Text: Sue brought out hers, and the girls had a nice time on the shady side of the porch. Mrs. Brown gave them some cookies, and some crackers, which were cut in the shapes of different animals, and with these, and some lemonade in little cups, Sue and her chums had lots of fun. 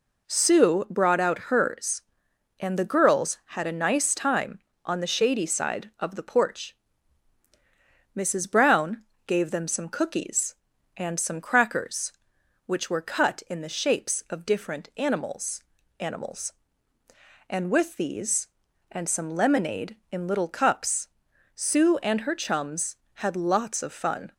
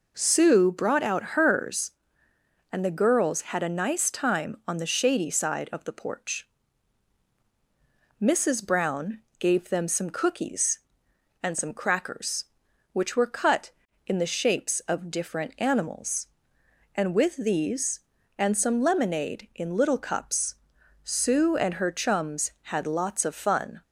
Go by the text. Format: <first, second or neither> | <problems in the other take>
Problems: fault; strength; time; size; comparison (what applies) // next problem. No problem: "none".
second | pauses between "Brown" and "gave"; slight; at 9.0 s; 0.24 s long; slight in the second // says "animals" twice; at 16.0 s